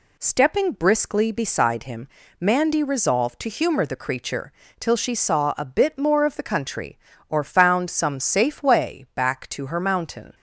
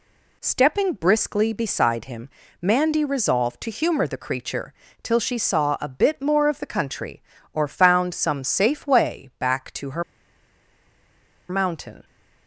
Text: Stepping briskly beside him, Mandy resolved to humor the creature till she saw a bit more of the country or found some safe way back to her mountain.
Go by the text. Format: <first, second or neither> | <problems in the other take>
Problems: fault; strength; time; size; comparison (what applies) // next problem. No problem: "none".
first | pauses between "creature" and "till"; slight; at 4.7 s; 0.28 s long; slight in the first // pauses between "her" and "mountain"; strong; at 10.0 s; 1.4 s long